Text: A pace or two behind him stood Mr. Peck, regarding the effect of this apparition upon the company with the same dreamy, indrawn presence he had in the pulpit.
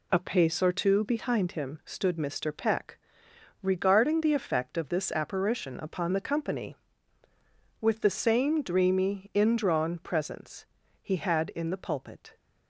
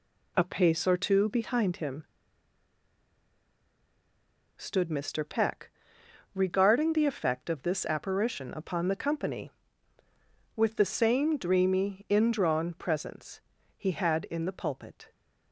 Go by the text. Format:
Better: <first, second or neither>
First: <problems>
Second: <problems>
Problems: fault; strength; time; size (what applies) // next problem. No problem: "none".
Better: first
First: pauses between "presence" and "he"; at 10.6 s; 0.38 s long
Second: pauses between "him" and "stood"; strong; at 2.0 s; 2.5 s long // pauses between "presence" and "he"; at 13.3 s; 0.38 s long